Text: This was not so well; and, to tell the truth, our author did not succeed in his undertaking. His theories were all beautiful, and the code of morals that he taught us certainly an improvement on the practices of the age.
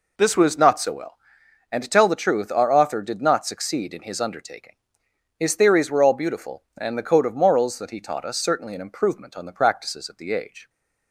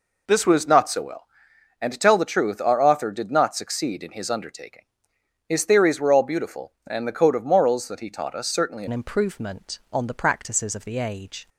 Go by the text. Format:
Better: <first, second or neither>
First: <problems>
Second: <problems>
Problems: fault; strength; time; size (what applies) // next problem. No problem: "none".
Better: first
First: none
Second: changes voice at "an"; from 8.8 s on; 2.6 s long